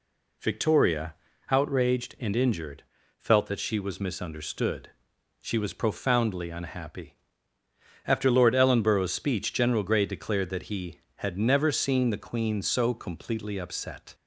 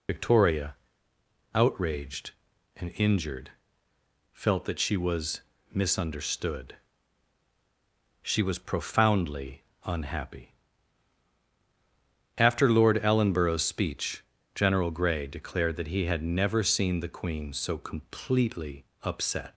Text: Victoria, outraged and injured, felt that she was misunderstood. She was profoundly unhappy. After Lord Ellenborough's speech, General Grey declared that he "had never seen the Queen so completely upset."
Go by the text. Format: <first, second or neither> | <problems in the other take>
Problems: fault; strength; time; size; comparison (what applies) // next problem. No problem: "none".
first | loses the start of "Victoria"; at 0.0 s; 75 ms // pauses between "was" and "misunderstood"; slight; at 5.4 s; 0.30 s long // pauses between "profoundly" and "unhappy"; slight; at 9.6 s; 0.22 s long // pauses between "completely" and "upset"; slight; at 18.8 s; 0.20 s long